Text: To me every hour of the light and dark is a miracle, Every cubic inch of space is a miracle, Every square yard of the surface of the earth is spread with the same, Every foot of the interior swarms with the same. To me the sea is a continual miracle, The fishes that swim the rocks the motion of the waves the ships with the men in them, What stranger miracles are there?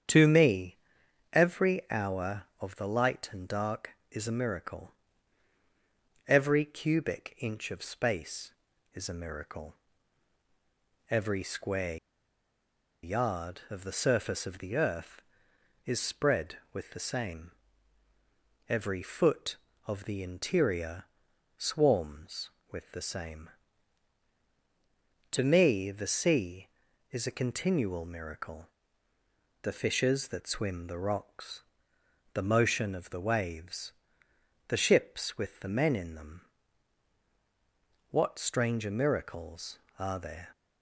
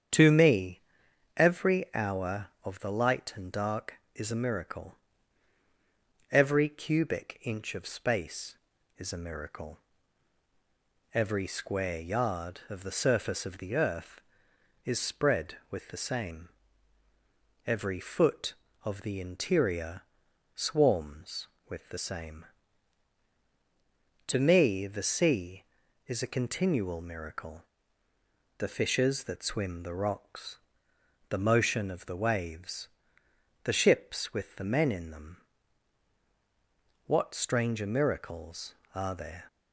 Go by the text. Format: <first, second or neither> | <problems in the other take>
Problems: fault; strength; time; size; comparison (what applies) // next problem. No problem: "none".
second | starts louder than the rest; strong; until 1.6 s; 8 dB; strong in the second // pauses between "me" and "every"; noticeable; at 0.7 s; 0.56 s long; noticeable in the second // pauses between "square" and "yard"; at 11.9 s; 1.0 s long // pauses between "interior" and "swarms"; noticeable; at 21.0 s; 0.52 s long; noticeable in the second // pauses between "rocks" and "the"; noticeable; at 31.6 s; 0.72 s long; noticeable in the second // pauses between "waves" and "the"; noticeable; at 33.9 s; 0.76 s long; noticeable in the second